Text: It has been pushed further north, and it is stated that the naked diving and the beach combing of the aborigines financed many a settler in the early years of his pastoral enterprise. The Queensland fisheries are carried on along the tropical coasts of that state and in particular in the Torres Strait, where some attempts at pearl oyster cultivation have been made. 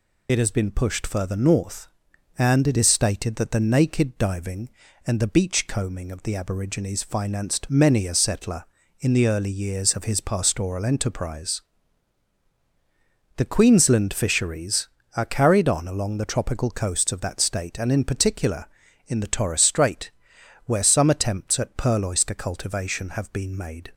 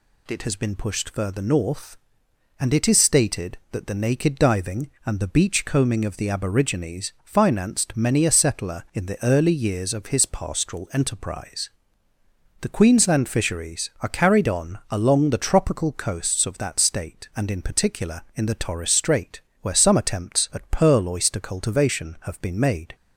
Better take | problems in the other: second | loses the start of "It"; at 0.2 s; 60 ms

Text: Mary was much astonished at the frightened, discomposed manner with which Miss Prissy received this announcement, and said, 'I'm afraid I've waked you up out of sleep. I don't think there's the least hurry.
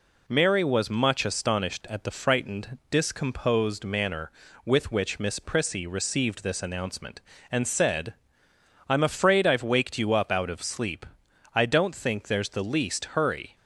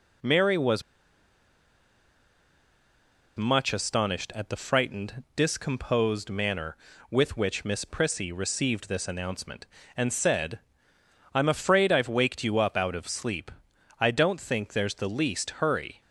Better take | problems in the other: first | pauses between "was" and "much"; strong; at 0.8 s; 2.5 s long

